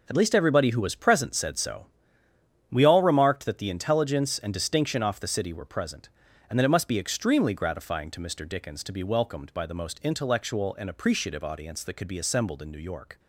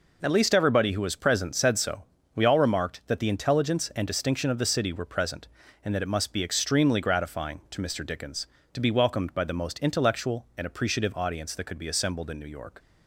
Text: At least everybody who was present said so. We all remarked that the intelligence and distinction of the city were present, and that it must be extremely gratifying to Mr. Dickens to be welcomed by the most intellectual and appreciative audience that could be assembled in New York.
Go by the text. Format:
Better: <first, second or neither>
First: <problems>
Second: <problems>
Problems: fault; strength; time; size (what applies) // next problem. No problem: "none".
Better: second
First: says "off" for "of"; at 5.0 s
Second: none